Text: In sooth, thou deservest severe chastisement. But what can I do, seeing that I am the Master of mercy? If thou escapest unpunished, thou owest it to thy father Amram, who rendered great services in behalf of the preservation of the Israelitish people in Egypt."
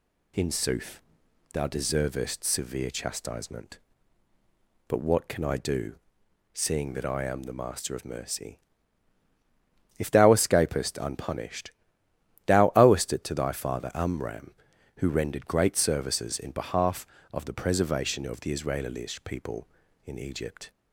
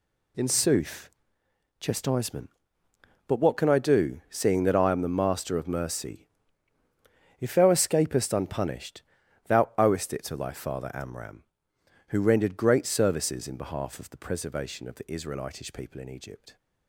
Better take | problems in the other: first | skips "thou deservest severe"; at 1.4 s

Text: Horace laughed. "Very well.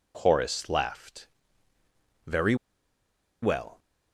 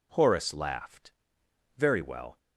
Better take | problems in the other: second | pauses between "Very" and "well"; noticeable; at 2.5 s; 0.86 s long

